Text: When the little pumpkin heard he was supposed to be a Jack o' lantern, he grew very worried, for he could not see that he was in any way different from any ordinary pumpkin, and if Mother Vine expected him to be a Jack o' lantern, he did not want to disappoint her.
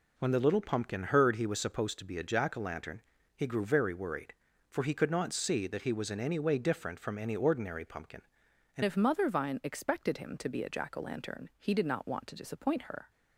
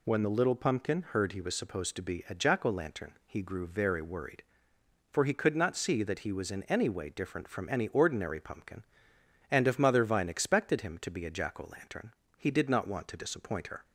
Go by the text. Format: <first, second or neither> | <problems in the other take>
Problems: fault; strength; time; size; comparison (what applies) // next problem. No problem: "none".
second | changes voice at "if"; from 8.8 s on; 4.2 s long